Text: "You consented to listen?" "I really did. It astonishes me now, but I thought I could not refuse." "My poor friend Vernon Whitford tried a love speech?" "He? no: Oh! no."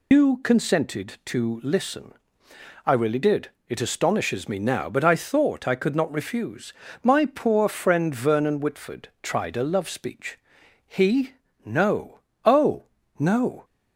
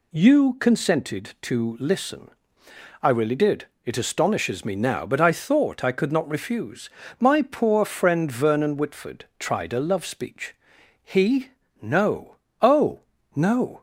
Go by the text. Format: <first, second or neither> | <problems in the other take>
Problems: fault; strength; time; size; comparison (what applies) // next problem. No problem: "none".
second | loses the start of "You"; at 0.1 s; 145 ms